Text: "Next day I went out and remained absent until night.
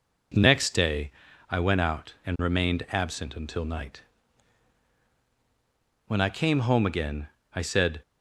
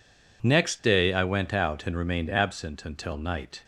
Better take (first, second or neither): second